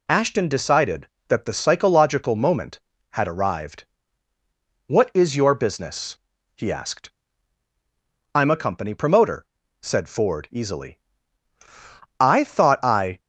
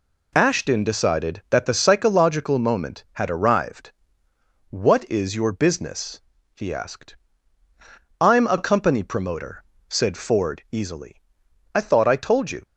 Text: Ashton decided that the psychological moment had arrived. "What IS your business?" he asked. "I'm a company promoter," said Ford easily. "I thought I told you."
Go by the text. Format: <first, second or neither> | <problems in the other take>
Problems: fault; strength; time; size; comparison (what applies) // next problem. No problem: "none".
second | stops before "told you"; at 13.1 s